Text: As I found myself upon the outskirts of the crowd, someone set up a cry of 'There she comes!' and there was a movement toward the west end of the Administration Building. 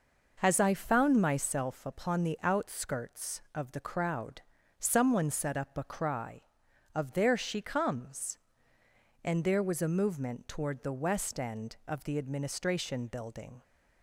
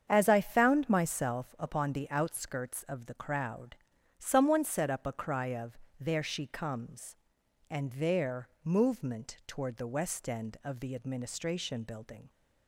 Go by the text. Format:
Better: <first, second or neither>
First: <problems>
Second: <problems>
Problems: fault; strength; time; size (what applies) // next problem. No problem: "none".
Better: first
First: none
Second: starts louder than the rest; strong; until 1.1 s; 7.5 dB // pauses between "of" and "There"; slight; at 5.7 s; 0.22 s long // skips "was a"; at 8.5 s